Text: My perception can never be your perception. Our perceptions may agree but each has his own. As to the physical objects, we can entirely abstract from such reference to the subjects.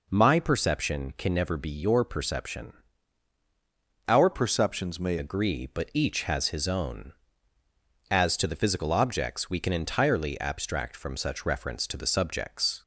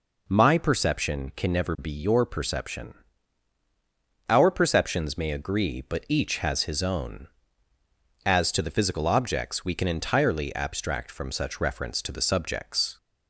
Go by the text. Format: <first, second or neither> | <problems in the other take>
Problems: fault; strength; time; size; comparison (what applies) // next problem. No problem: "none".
second | changes voice from "perceptions" to "may"; from 4.3 to 5.1 s; 0.8 s long